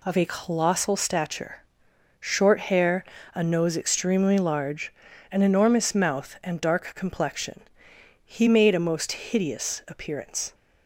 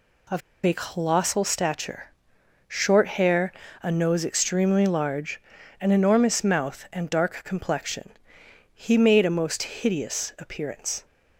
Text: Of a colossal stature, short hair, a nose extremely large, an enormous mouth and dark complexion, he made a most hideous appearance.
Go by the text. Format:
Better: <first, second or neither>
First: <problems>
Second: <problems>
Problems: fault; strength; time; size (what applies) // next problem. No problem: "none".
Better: first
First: none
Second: pauses between "Of" and "a"; slight; at 0.4 s; 0.24 s long